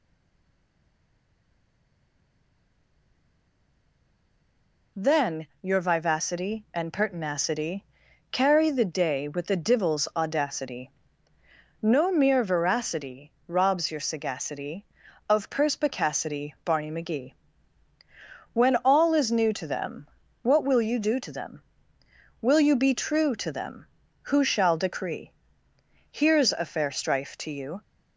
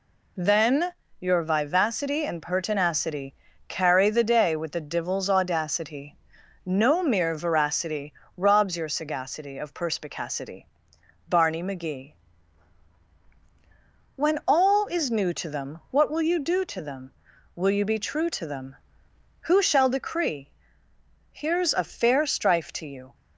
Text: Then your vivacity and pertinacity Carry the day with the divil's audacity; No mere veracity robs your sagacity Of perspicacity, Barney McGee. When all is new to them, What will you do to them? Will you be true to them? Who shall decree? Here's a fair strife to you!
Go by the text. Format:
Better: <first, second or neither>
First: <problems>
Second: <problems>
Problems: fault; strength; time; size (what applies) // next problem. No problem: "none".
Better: second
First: stays silent before the first word; strong; until 4.9 s; 4.9 s long // pauses between "Then" and "your"; slight; at 5.4 s; 0.16 s long // pauses between "pertinacity" and "Carry"; noticeable; at 7.8 s; 0.48 s long // pauses between "veracity" and "robs"; slight; at 13.3 s; 0.16 s long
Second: pauses between "Then" and "your"; slight; at 0.9 s; 0.26 s long // pauses between "pertinacity" and "Carry"; slight; at 3.3 s; 0.36 s long // pauses between "veracity" and "robs"; slight; at 8.1 s; 0.24 s long